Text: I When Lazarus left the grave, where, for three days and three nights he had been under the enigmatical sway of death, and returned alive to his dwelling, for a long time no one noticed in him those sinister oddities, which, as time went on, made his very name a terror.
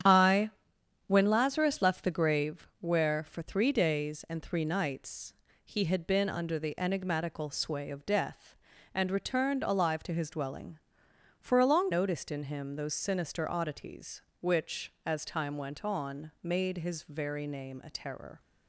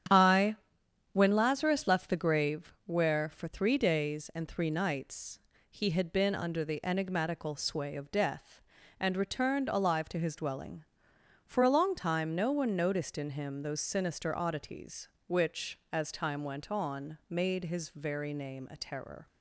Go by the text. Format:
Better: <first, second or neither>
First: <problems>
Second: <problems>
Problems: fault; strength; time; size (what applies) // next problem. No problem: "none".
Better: second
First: starts louder than the rest; strong; until 1.6 s; 9 dB // pauses between "I" and "When"; noticeable; at 0.4 s; 0.56 s long // pauses between "nights" and "he"; slight; at 5.3 s; 0.30 s long // skips "time no one"; at 11.9 s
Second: starts louder than the rest; strong; until 1.6 s; 9.5 dB // pauses between "I" and "When"; noticeable; at 0.5 s; 0.56 s long // pauses between "nights" and "he"; slight; at 5.3 s; 0.30 s long